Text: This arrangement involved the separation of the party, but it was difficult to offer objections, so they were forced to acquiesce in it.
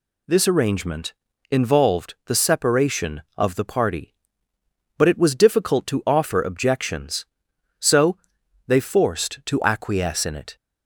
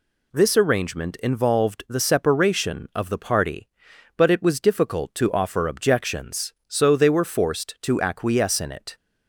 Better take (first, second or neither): second